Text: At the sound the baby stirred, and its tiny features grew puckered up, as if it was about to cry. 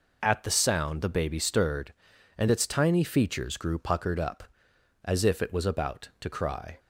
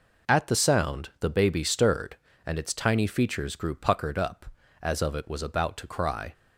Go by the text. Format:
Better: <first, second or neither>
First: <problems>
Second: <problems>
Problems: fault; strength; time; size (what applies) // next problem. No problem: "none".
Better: first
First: none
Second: says "of" for "if"; at 5.0 s